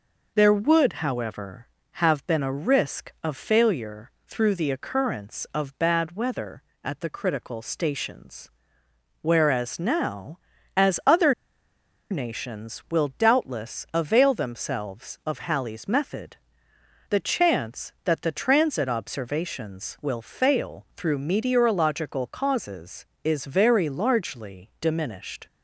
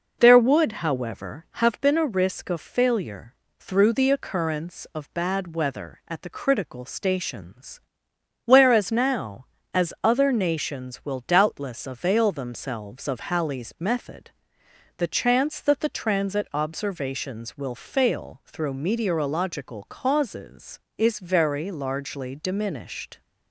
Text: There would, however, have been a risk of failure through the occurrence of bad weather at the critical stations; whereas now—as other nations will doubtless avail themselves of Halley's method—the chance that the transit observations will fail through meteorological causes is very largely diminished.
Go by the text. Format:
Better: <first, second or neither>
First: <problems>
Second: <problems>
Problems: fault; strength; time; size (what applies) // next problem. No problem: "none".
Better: second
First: pauses between "failure" and "through"; slight; at 4.1 s; 0.16 s long // pauses between "other" and "nations"; noticeable; at 11.3 s; 0.77 s long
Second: pauses between "failure" and "through"; slight; at 3.3 s; 0.26 s long